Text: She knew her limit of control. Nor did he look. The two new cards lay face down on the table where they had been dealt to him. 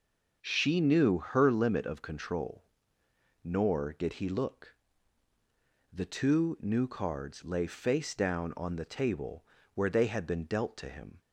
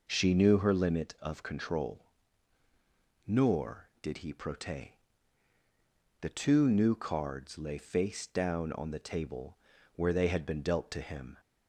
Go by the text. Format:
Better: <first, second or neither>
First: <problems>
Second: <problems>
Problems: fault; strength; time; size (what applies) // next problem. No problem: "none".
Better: first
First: pauses between "table" and "where"; slight; at 9.4 s; 0.30 s long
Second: says "prote" for "look"; at 4.3 s // pauses between "table" and "where"; at 9.5 s; 0.40 s long